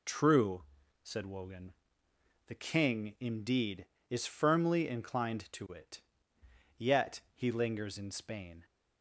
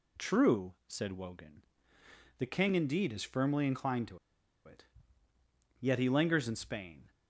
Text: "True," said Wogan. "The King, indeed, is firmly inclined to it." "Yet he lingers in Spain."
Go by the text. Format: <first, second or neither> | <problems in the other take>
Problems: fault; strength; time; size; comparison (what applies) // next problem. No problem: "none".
first | pauses between "to" and "it"; noticeable; at 4.1 s; 0.47 s long